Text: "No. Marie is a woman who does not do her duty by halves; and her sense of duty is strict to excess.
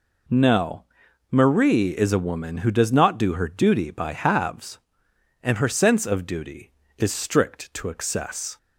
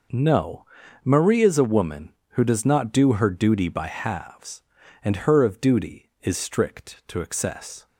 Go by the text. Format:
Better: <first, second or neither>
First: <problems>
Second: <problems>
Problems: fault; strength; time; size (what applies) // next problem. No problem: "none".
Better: first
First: none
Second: skips "sense"; at 5.4 s